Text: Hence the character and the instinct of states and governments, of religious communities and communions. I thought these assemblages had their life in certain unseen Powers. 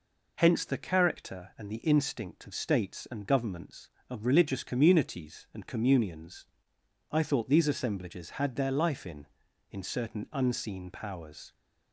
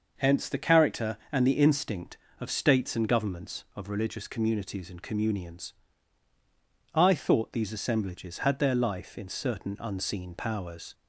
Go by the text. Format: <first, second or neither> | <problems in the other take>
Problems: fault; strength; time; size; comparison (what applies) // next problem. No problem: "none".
second | says "in" twice; at 9.6 s